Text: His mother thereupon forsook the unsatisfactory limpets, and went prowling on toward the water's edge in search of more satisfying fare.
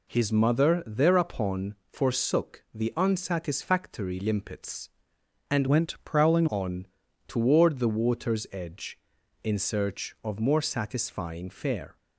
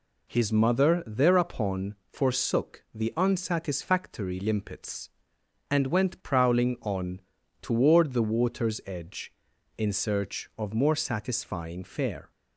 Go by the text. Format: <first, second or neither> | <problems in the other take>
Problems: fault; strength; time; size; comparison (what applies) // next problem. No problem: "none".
second | changes voice from "went" to "prowling"; from 5.6 to 6.4 s; 0.8 s long // pauses between "on" and "toward"; at 6.8 s; 0.40 s long; also in the second